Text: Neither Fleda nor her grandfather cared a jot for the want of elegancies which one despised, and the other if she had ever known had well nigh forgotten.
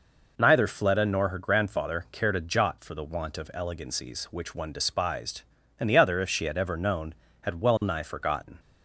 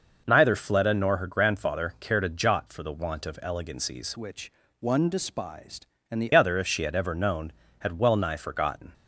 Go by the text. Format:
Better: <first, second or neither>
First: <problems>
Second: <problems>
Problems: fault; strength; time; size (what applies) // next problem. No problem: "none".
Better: first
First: none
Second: changes voice from "which" to "the"; from 4.1 to 6.3 s; 2.2 s long // pauses between "which" and "one"; slight; at 4.5 s; 0.28 s long